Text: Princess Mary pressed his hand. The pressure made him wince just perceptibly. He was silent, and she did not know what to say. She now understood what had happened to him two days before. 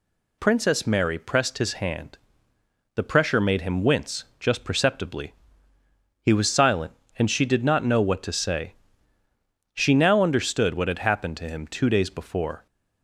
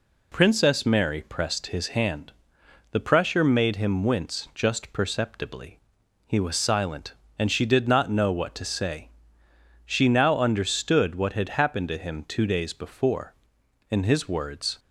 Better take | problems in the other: first | goes on to say "In his words"; noticeable; from 13.9 s on; 0.88 s long

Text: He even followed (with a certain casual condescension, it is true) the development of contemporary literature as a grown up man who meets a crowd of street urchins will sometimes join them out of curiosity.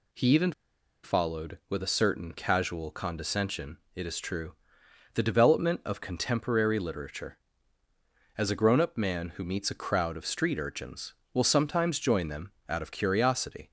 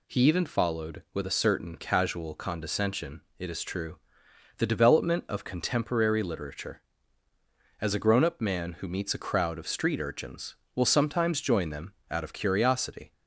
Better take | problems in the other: second | pauses between "even" and "followed"; noticeable; at 0.5 s; 0.52 s long // pauses between "them" and "out"; slight; at 12.5 s; 0.16 s long; slight in the second

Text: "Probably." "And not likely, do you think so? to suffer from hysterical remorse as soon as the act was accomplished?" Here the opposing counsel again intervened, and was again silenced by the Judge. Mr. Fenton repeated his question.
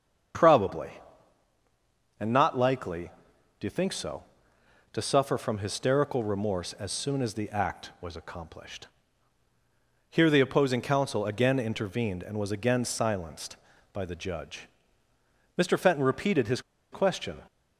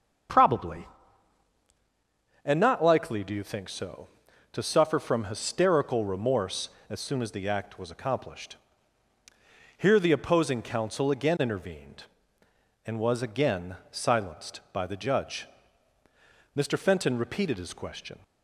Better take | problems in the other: second | starts louder than the rest; strong; until 2.6 s; 7.5 dB; also in the second // pauses between "his" and "question"; slight; at 16.5 s; 0.32 s long

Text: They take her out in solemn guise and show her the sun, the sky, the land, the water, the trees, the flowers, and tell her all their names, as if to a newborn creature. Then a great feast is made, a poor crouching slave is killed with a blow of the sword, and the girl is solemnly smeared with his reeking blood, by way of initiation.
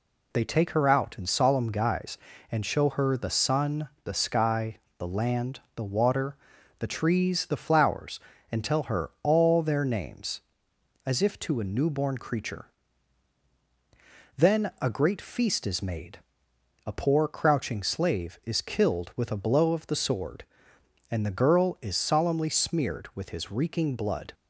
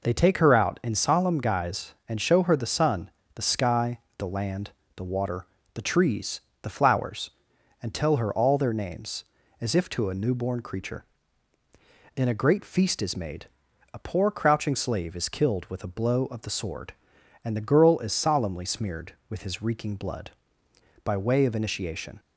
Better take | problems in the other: second | stops before "by way of initiation"; at 24.3 s

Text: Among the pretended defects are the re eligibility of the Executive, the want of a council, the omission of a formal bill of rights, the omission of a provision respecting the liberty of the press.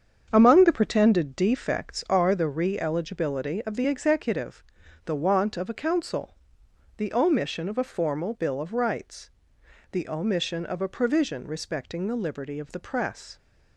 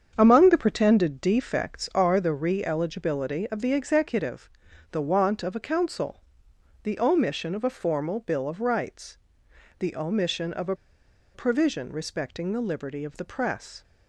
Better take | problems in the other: first | starts louder than the rest; strong; until 1.1 s; 7.5 dB; strong in the first // pauses between "a" and "provision"; noticeable; at 10.7 s; 0.59 s long

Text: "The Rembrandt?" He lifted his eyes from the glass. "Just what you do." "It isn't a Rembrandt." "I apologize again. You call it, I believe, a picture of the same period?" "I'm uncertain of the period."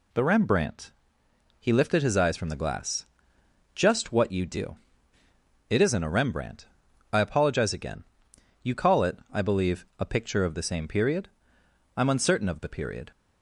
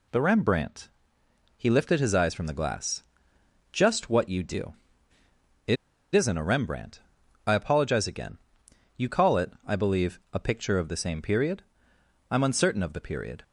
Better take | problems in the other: first | pauses between "It" and "isn't"; at 5.7 s; 0.38 s long

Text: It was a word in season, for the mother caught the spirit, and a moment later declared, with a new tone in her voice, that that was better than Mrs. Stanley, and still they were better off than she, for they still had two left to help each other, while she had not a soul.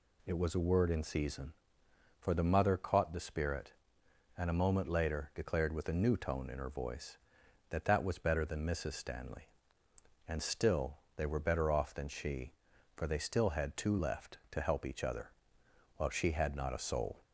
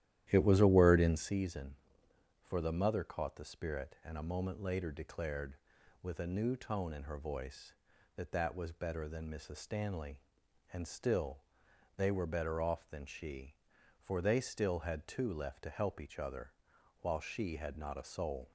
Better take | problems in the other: first | starts louder than the rest; strong; until 1.4 s; 12.5 dB // pauses between "still" and "they"; noticeable; at 11.3 s; 0.58 s long; slight in the first

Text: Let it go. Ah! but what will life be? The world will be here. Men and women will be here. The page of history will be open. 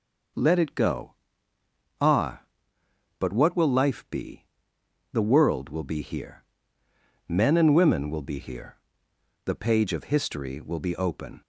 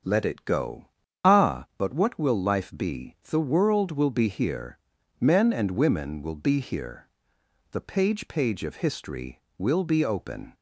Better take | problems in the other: first | starts louder than the rest; strong; until 1.4 s; 7.5 dB // says "page" twice; at 8.2 s

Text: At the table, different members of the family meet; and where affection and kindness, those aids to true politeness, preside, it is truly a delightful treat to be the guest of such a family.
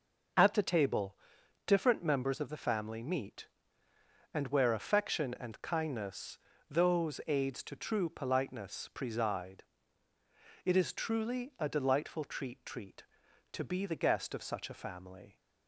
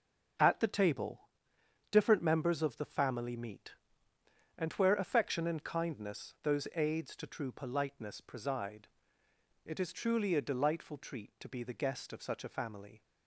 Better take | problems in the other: second | starts louder than the rest; noticeable; until 1.8 s; 6 dB // says "treat" twice; at 12.6 s

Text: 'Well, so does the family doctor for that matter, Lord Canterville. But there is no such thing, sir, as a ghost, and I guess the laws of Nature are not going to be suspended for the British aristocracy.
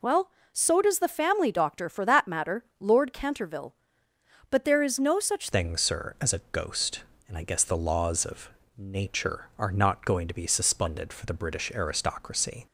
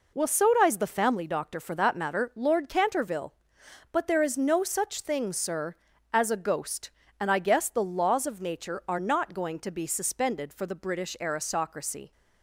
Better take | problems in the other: second | changes voice at "thing"; from 5.5 s on; 7.1 s long // pauses between "of" and "Nature"; slight; at 8.4 s; 0.28 s long

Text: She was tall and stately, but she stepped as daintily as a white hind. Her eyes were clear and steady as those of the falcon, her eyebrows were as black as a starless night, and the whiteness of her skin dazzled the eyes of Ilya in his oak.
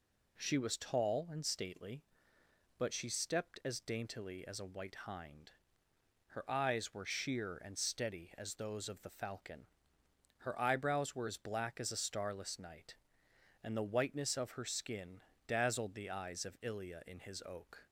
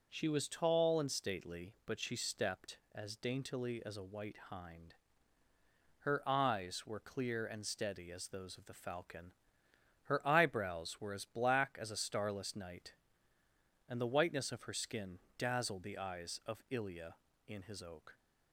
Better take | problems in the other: second | says "sheer" for "clear"; at 7.0 s // pauses between "skin" and "dazzled"; slight; at 15.2 s; 0.26 s long; slight in the second

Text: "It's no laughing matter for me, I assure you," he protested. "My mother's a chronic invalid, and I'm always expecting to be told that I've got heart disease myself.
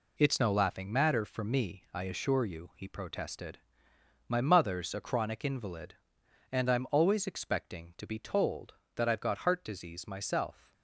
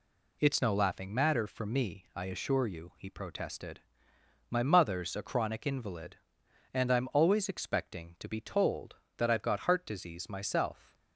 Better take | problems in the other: second | gets quieter; throughout; 7 dB

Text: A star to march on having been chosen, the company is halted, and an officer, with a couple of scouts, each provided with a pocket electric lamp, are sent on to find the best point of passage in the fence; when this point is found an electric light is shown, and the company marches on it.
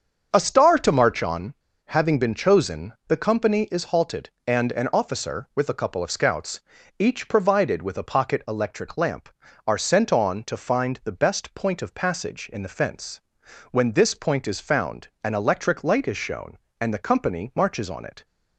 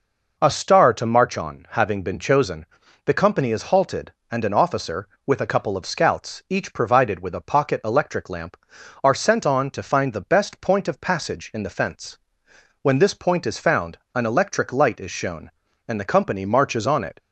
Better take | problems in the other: second | starts louder than the rest; until 1.3 s; 7 dB // pauses between "on" and "having"; slight; at 1.5 s; 0.30 s long // pauses between "found" and "an"; slight; at 15.0 s; 0.16 s long; slight in the second

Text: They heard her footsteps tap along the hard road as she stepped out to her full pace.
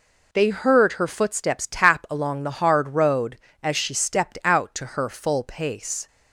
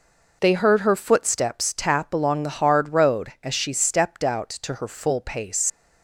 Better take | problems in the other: first | leaves "pace" unfinished; at 5.6 s; 100 ms

